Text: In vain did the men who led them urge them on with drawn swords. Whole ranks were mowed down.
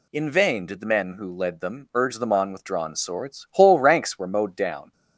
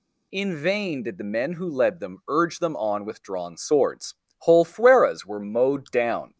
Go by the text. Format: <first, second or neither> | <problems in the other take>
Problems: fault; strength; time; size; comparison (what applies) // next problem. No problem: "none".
first | says "fueras" for "ranks"; at 4.6 s